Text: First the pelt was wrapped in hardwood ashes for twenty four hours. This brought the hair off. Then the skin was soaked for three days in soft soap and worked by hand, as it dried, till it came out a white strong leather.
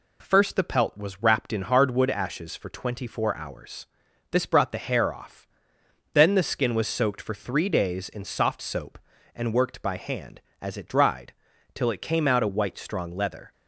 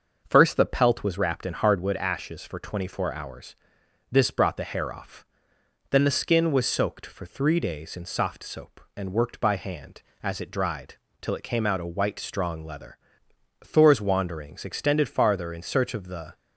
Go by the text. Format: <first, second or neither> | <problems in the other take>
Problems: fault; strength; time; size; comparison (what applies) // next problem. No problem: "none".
first | starts louder than the rest; until 1.2 s; 6.5 dB // goes on to say "Thor's wanderings extended farther in search of the"; strong; from 13.6 s on; 2.7 s long